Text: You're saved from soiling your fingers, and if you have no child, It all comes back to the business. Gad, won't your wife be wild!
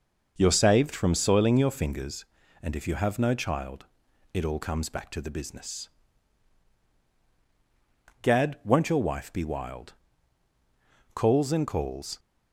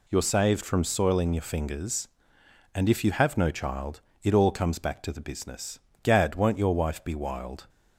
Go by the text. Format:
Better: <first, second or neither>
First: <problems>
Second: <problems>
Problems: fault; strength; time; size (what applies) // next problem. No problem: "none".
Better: second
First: goes on to say "Calls and calls"; noticeable; from 11.1 s on; 1.0 s long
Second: none